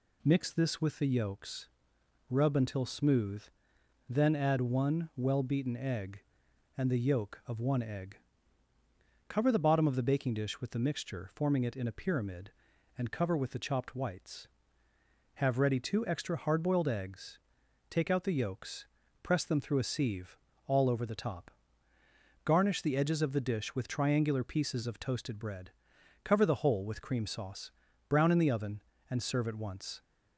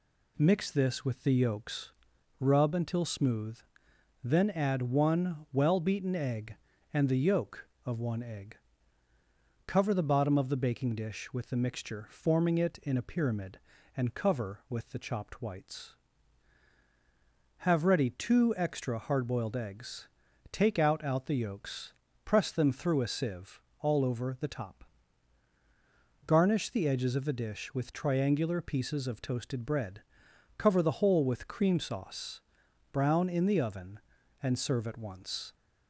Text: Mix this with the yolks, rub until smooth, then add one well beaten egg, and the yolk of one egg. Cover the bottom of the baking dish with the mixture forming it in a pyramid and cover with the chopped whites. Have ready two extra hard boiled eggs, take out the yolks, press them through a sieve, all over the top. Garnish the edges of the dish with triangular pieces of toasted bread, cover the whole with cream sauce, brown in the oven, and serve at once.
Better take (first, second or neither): first